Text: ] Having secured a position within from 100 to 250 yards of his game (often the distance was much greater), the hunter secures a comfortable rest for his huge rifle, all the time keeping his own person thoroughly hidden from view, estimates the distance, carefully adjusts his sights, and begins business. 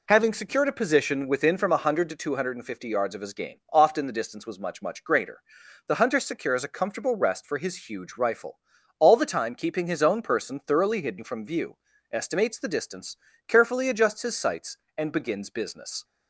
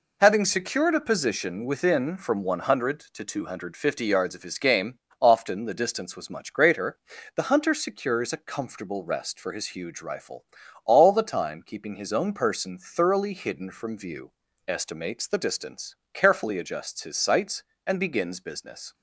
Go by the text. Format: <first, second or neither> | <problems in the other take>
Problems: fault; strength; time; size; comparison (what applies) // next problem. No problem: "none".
second | says "much" twice; at 4.8 s